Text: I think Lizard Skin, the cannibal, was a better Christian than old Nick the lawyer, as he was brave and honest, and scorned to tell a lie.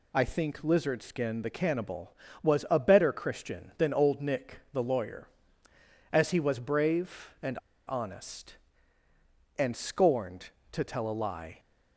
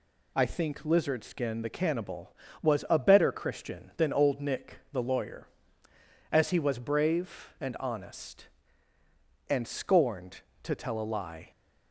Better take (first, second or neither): second